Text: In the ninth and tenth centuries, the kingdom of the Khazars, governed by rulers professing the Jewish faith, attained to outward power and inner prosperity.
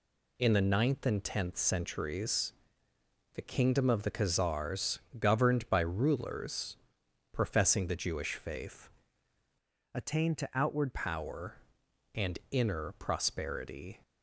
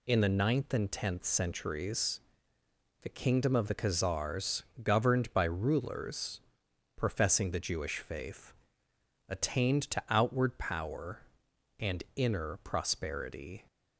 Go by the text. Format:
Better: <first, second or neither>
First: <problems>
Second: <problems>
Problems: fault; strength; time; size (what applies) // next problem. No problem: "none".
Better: second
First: pauses between "rulers" and "professing"; noticeable; at 6.7 s; 0.56 s long // changes voice from "attained" to "outward"; from 9.9 to 10.9 s; 1.0 s long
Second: pauses between "rulers" and "professing"; noticeable; at 6.3 s; 0.56 s long